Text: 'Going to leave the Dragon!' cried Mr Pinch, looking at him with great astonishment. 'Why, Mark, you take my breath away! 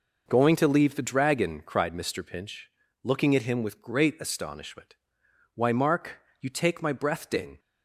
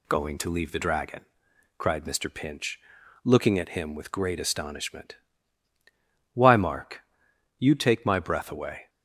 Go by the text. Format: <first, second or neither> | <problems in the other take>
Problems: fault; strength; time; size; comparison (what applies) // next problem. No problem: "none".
second | says "ding" for "away"; at 7.2 s